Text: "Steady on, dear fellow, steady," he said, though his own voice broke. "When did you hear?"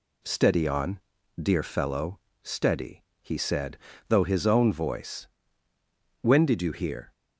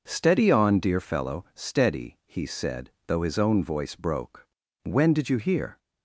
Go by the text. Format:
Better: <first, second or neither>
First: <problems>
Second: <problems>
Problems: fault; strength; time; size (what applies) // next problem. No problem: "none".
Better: second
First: skips "broke"; at 5.7 s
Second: none